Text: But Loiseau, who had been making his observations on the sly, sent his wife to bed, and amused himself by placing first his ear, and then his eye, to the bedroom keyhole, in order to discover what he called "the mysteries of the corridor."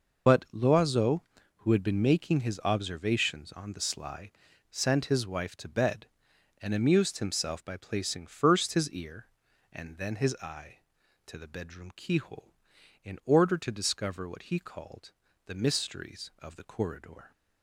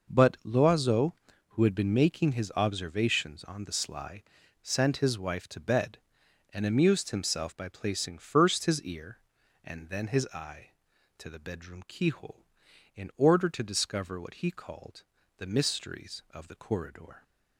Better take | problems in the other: second | loses the start of "But"; at 0.2 s; 90 ms // pauses between "called" and "the"; slight; at 15.1 s; 0.34 s long; slight in the second

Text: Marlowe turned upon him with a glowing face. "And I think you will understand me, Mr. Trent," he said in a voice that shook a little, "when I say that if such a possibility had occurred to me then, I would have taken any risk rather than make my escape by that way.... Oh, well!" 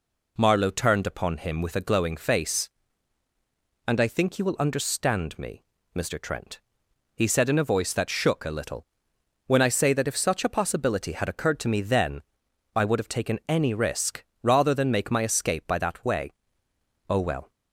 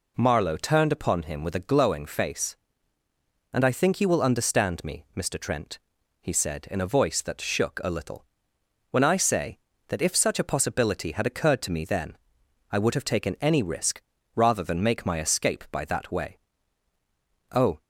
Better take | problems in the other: first | pauses between "risk" and "rather"; slight; at 14.0 s; 0.35 s long; slight in the first // stops before "well"; at 17.8 s

